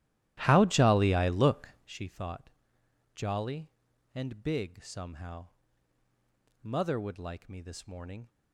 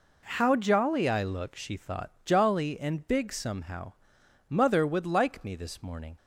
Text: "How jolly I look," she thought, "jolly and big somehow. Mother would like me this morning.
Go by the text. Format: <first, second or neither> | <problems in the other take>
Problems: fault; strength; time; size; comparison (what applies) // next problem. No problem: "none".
second | starts louder than the rest; strong; until 2.0 s; 14.5 dB